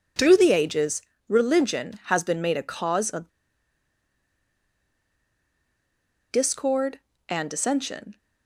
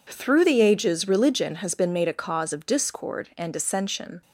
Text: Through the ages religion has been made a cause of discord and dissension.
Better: second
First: pauses between "ages" and "religion"; slight; at 1.0 s; 0.28 s long // pauses between "of" and "discord"; strong; at 3.3 s; 3.0 s long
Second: none

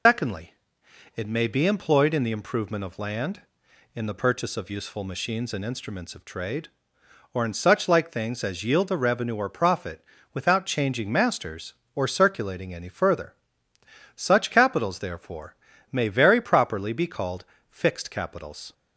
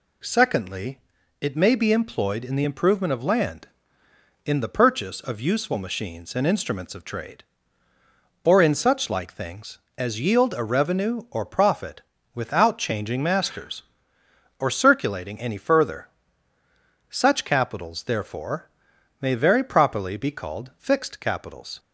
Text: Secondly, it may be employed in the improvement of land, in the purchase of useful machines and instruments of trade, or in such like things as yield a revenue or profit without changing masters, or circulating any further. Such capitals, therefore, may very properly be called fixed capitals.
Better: second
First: loses the start of "Secondly"; at 0.0 s; 135 ms // pauses between "profit" and "without"; slight; at 10.0 s; 0.28 s long // pauses between "called" and "fixed"; slight; at 17.4 s; 0.28 s long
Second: pauses between "profit" and "without"; slight; at 12.0 s; 0.34 s long

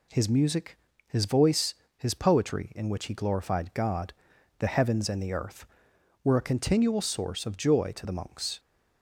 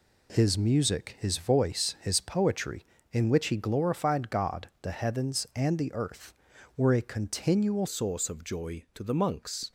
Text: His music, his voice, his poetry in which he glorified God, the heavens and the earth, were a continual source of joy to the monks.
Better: first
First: none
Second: changes voice at "source"; from 7.8 s on; 1.9 s long

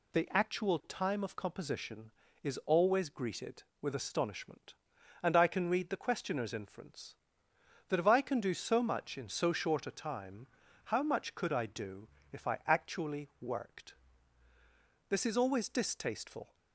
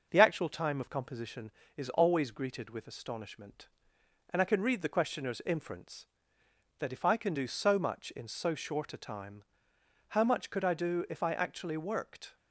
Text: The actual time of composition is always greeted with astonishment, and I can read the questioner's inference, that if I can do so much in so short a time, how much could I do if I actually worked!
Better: second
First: pauses between "do" and "if"; slight; at 12.0 s; 0.24 s long // goes on to say "This is always distasteful"; from 15.0 s on; 1.4 s long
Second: none

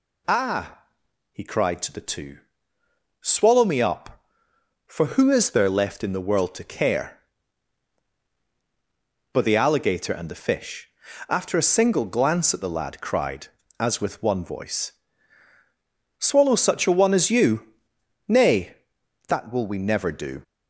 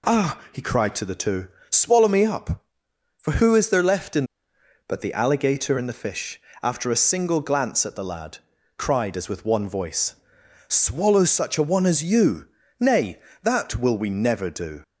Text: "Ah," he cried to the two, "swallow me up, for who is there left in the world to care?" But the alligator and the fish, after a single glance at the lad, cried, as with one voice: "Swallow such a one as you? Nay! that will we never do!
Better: first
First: none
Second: skips "the world to care"; at 4.5 s

